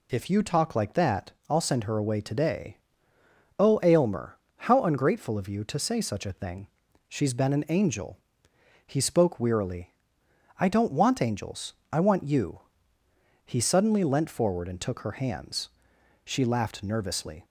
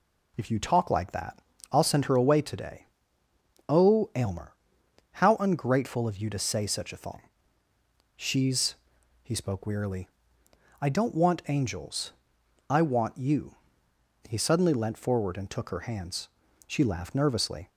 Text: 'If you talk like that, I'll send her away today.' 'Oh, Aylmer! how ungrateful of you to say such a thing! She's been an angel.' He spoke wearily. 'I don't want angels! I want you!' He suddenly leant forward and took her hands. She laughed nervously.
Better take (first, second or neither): first